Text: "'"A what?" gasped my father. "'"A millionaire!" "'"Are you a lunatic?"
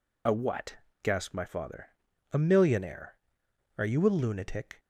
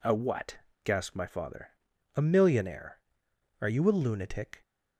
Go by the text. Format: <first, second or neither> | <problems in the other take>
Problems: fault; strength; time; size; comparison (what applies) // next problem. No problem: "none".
second | loses the start of "A"; at 0.2 s; 40 ms